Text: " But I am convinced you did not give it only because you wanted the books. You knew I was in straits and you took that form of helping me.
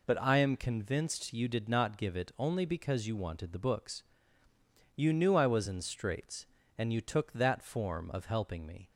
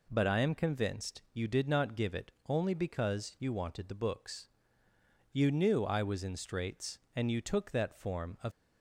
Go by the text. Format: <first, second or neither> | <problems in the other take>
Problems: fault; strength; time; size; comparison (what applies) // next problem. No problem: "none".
first | pauses between "it" and "only"; slight; at 2.3 s; 0.16 s long // stops before "helping me"; at 8.5 s